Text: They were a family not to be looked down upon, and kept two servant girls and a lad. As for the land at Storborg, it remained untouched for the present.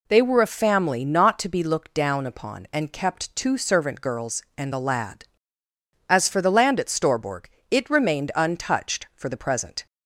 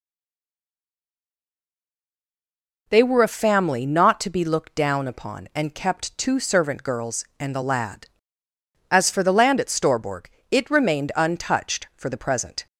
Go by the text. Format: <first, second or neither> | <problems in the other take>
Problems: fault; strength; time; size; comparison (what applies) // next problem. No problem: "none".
first | stays silent before the first word; strong; until 2.8 s; 2.8 s long